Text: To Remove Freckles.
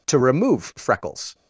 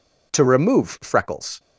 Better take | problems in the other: neither | none

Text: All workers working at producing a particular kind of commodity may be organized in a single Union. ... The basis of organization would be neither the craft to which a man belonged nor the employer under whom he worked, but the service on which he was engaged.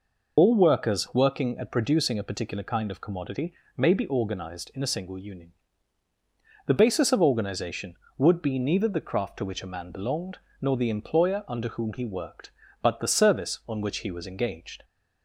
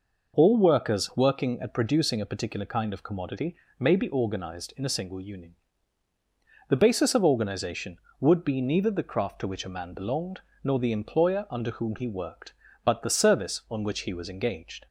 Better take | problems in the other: second | loses the start of "All"; at 0.3 s; 65 ms // pauses between "commodity" and "may"; slight; at 3.5 s; 0.24 s long; slight in the second // pauses between "belonged" and "nor"; slight; at 10.3 s; 0.22 s long; slight in the second

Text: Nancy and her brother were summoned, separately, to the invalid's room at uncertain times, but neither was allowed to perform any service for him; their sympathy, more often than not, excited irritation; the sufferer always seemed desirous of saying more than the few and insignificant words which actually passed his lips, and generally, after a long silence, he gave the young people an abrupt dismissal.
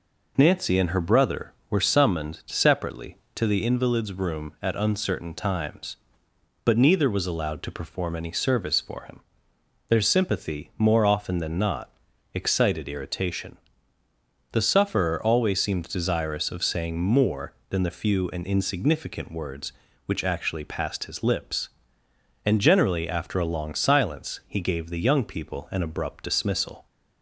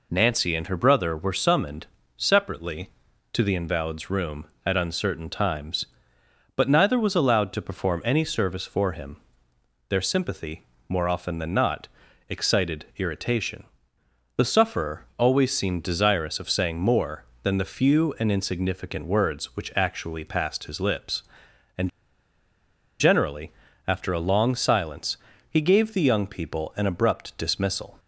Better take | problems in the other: first | pauses between "and" and "generally"; at 21.8 s; 1.1 s long

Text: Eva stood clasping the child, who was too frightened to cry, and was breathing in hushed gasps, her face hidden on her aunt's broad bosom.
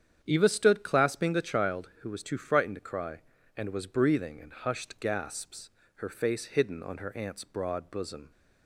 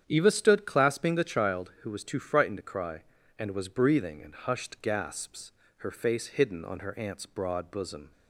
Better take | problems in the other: neither | starts louder than the rest; strong; the same in both

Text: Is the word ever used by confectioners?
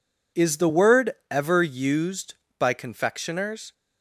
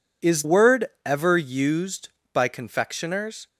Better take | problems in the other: first | skips "the"; at 0.4 s // pauses between "word" and "ever"; slight; at 0.8 s; 0.18 s long; slight in the first

